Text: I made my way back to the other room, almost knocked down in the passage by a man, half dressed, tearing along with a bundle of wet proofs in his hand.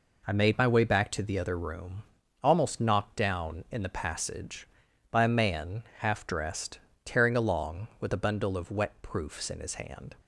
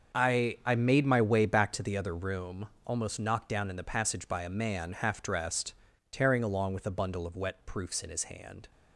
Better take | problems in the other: first | starts louder than the rest; until 1.2 s; 7 dB // says "I" twice; at 0.6 s

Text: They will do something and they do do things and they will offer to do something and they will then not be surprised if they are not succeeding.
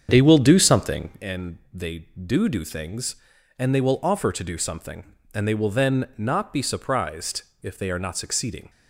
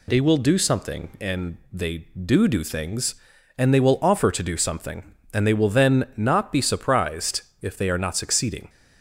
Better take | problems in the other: second | starts louder than the rest; strong; until 1.2 s; 8 dB // pauses between "surprised" and "if"; slight; at 7.4 s; 0.18 s long; slight in the second

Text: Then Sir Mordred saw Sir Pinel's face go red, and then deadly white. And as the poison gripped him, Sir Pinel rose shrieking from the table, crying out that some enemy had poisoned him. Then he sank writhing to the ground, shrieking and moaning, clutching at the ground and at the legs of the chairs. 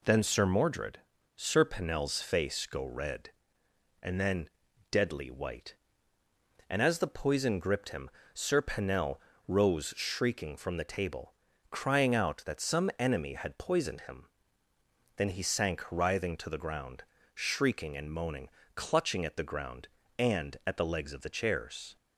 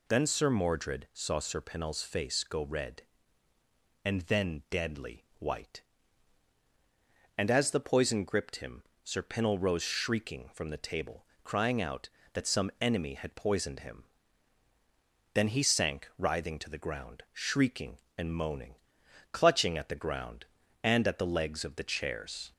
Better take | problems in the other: second | skips "saw"; at 1.1 s // pauses between "then" and "deadly"; at 4.4 s; 0.42 s long // pauses between "Pinel" and "rose"; slight; at 9.1 s; 0.28 s long

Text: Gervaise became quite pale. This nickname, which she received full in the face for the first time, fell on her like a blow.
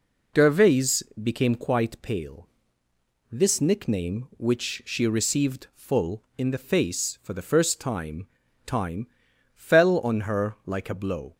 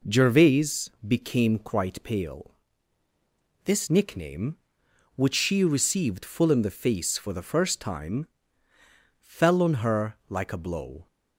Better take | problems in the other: second | pauses between "Gervaise" and "became"; slight; at 1.0 s; 0.20 s long; slight in the second // says "time" twice; at 8.6 s

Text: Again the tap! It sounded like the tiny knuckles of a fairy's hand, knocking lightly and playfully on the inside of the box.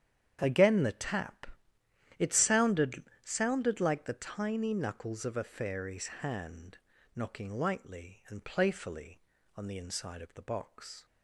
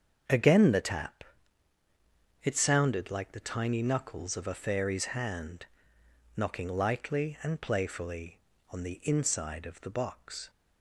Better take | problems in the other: second | starts louder than the rest; strong; until 1.4 s; 9 dB; strong in the second // says "sounded" twice; at 3.2 s // pauses between "fairy's" and "hand"; slight; at 6.0 s; 0.16 s long

